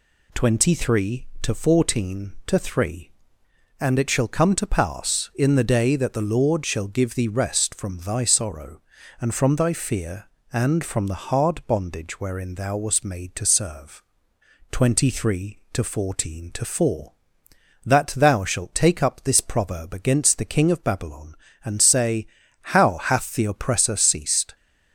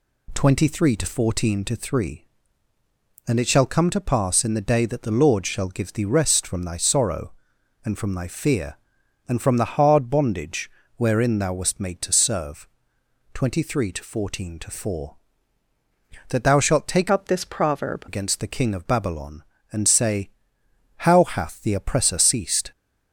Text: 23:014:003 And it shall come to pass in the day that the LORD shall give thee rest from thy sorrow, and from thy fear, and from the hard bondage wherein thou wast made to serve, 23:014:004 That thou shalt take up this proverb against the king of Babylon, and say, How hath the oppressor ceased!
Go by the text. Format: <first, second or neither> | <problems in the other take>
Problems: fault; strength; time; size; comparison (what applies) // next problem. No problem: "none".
first | pauses between "bondage" and "wherein"; slight; at 10.7 s; 0.24 s long // changes voice from "up" to "proverb"; from 17.1 to 18.0 s; 0.9 s long